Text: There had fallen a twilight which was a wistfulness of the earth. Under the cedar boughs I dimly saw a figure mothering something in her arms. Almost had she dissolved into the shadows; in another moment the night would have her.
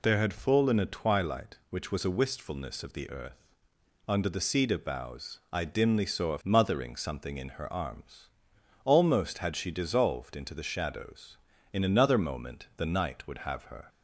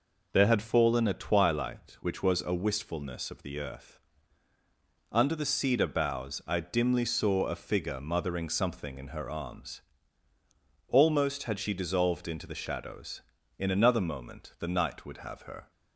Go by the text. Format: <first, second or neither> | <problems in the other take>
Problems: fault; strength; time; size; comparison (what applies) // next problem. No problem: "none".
second | skips "figure"; at 6.4 s